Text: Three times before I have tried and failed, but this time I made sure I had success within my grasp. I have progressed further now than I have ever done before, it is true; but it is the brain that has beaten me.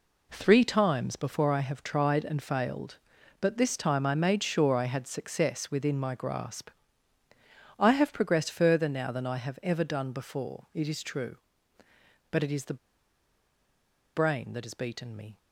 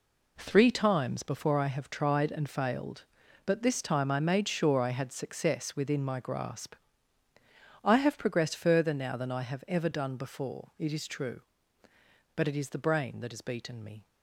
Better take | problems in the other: second | pauses between "the" and "brain"; strong; at 12.7 s; 1.3 s long

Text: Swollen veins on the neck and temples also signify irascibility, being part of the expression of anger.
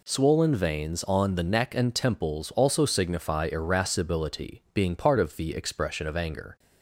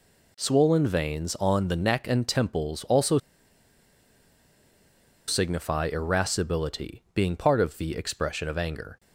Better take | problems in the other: first | pauses between "also" and "signify"; strong; at 3.1 s; 2.0 s long

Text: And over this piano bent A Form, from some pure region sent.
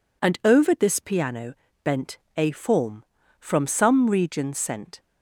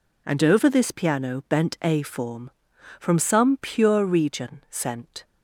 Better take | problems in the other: second | pauses between "piano" and "bent"; slight; at 1.5 s; 0.30 s long // pauses between "bent" and "A"; slight; at 2.1 s; 0.18 s long // skips "pure"; at 4.0 s

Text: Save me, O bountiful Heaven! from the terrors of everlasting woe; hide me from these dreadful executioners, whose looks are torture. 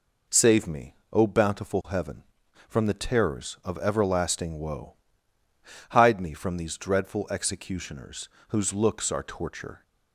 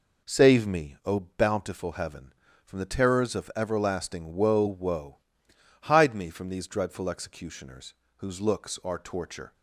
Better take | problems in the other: first | says "woe" twice; at 4.6 s

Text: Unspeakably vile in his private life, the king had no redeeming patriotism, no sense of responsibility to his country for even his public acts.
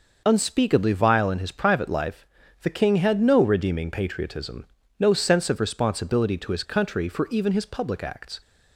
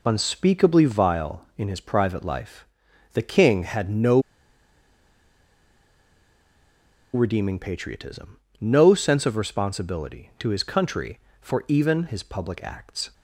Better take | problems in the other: first | pauses between "no" and "redeeming"; strong; at 4.1 s; 2.9 s long

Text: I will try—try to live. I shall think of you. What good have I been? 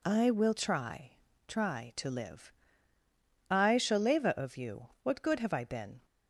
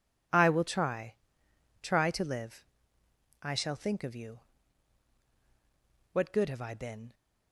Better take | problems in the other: second | says "leva" for "think"; at 3.9 s

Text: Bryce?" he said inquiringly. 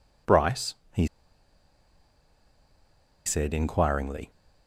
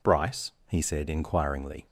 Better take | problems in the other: second | pauses between "he" and "said"; strong; at 1.0 s; 2.1 s long

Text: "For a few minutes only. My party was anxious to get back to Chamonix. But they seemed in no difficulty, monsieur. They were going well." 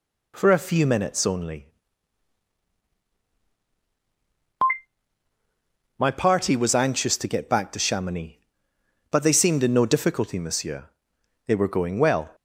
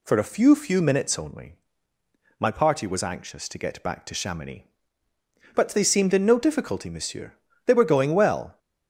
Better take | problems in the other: first | says "few" twice; at 0.5 s

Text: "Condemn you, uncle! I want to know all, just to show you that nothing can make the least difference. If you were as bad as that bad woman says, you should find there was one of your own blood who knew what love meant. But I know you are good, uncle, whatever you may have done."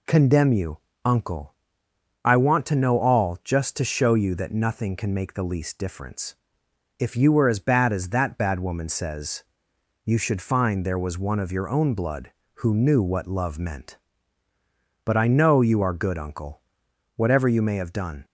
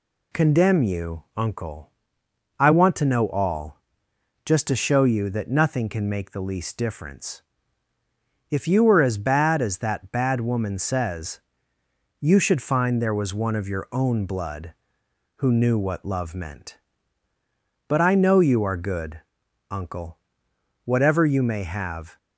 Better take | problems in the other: first | stops before "done"; at 22.1 s

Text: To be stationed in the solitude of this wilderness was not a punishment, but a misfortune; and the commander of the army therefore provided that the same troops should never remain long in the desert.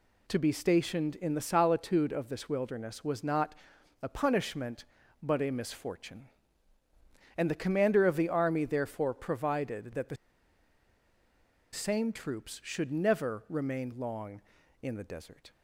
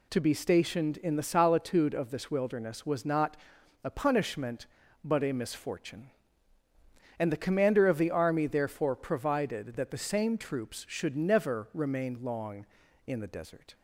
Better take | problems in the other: second | pauses between "not" and "a"; noticeable; at 3.5 s; 0.48 s long; noticeable in the second // pauses between "the" and "same"; strong; at 10.1 s; 1.5 s long

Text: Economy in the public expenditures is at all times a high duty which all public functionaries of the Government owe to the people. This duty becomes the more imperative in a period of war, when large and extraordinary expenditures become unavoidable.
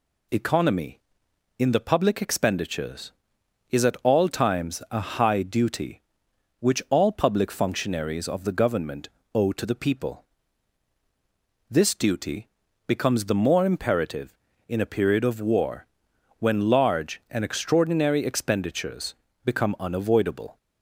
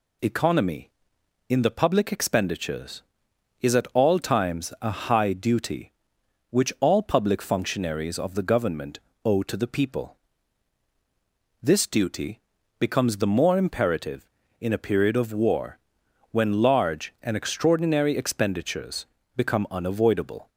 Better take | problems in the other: neither | pauses between "a" and "high"; slight; the same in both // pauses between "Government" and "owe"; slight; the same in both // pauses between "duty" and "becomes"; the same in both // pauses between "expenditures" and "become"; slight; the same in both

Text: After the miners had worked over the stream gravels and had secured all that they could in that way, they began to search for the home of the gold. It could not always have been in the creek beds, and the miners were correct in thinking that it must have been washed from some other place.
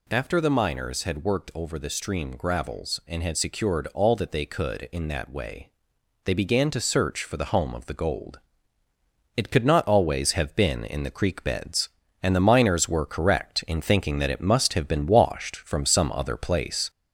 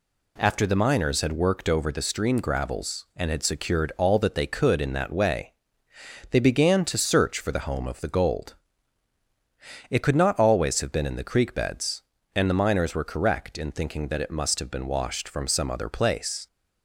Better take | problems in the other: second | gets louder; slight; throughout; 3.5 dB

